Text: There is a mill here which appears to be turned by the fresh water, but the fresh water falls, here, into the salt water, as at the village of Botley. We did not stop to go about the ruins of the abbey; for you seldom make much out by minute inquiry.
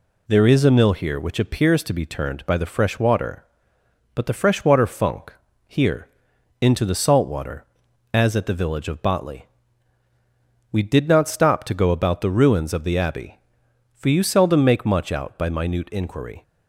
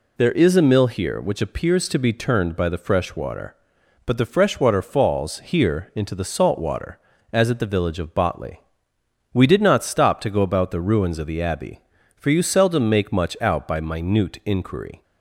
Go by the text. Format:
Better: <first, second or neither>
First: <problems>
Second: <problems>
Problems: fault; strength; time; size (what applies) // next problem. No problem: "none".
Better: second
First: says "funk" for "falls"; at 4.8 s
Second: none